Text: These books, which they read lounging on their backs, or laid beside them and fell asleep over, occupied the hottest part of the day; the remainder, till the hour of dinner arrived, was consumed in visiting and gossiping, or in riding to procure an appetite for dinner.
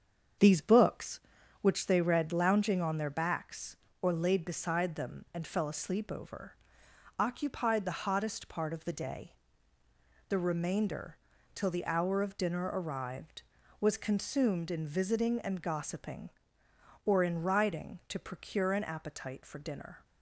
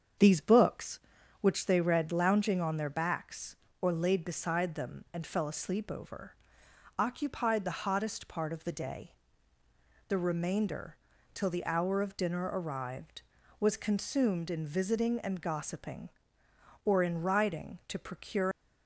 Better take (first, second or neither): first